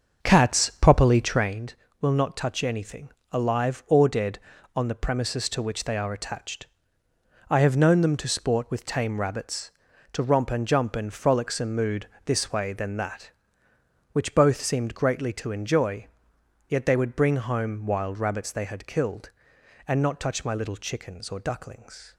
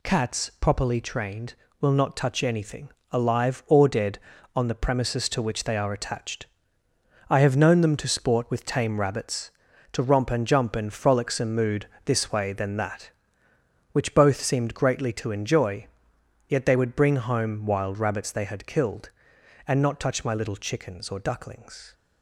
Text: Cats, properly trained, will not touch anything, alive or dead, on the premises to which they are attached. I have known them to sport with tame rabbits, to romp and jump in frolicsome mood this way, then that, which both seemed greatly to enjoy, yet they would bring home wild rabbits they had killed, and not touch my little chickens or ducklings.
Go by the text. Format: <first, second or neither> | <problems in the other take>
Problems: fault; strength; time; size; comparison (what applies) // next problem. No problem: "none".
second | starts louder than the rest; until 1.7 s; 6.5 dB // pauses between "mood" and "this"; slight; at 12.0 s; 0.20 s long; slight in the second